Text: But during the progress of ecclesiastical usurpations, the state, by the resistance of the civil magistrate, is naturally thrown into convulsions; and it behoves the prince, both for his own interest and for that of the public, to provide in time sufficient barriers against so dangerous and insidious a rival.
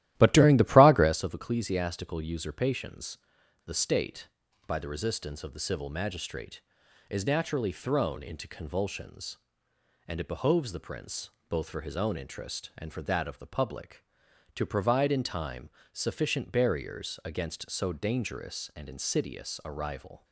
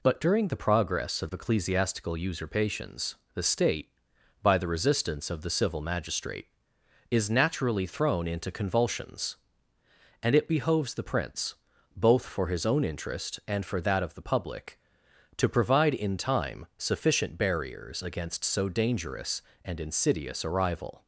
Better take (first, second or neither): second